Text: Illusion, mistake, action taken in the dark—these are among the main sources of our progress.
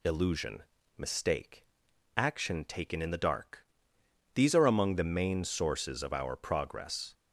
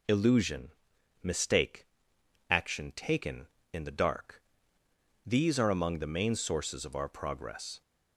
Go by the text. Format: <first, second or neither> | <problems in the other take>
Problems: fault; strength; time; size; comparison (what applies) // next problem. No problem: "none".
neither | none